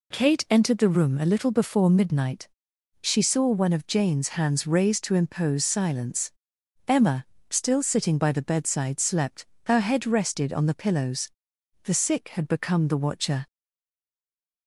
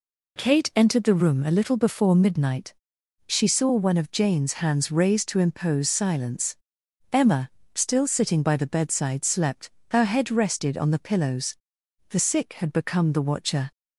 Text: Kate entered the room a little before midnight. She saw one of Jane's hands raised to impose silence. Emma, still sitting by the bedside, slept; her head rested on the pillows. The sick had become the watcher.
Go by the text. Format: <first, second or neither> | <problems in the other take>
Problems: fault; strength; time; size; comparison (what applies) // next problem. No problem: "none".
second | stays silent after the last word; noticeable; from 13.4 s on; 1.2 s long